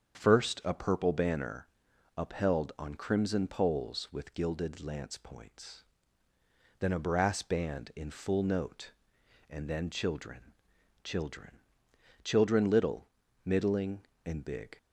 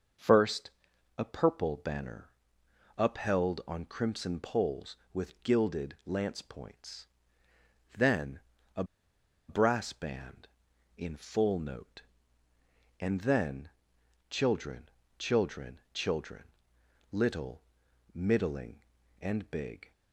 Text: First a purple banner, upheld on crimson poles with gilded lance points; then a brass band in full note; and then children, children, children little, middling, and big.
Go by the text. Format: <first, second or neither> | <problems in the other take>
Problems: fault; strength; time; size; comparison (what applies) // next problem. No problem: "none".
first | starts louder than the rest; until 1.6 s; 6.5 dB; strong in the first // pauses between "First" and "a"; noticeable; at 0.6 s; 0.48 s long // pauses between "then" and "a"; slight; at 8.4 s; 0.34 s long // pauses between "a" and "brass"; noticeable; at 8.8 s; 0.65 s long // pauses between "then" and "children"; noticeable; at 13.6 s; 0.58 s long // pauses between "children" and "little"; noticeable; at 16.4 s; 0.66 s long